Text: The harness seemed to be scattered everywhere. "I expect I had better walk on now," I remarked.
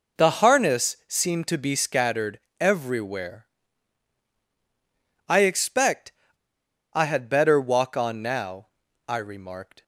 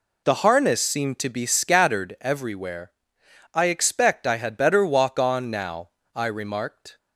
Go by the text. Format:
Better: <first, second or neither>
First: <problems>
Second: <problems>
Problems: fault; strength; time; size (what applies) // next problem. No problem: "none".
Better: second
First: pauses between "scattered" and "everywhere"; slight; at 2.3 s; 0.18 s long // pauses between "expect" and "I"; noticeable; at 6.1 s; 0.81 s long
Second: none